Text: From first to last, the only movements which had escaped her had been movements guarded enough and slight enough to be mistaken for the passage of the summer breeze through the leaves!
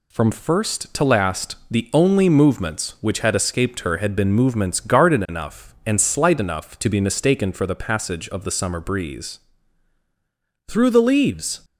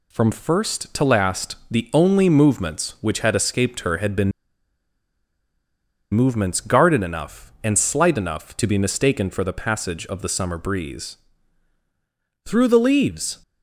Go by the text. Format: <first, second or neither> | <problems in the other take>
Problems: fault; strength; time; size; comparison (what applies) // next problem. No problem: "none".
first | pauses between "been" and "movements"; strong; at 4.3 s; 1.8 s long // pauses between "breeze" and "through"; strong; at 11.1 s; 1.2 s long; strong in the first